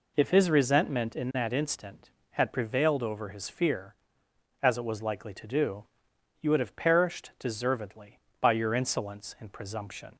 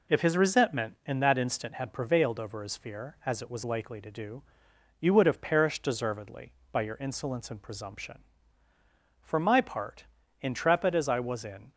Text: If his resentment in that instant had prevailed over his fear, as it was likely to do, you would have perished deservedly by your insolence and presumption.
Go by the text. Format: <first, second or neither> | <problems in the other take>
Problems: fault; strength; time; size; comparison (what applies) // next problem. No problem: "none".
first | goes on to say "For my part intrepid as I was in"; strong; from 9.2 s on; 2.5 s long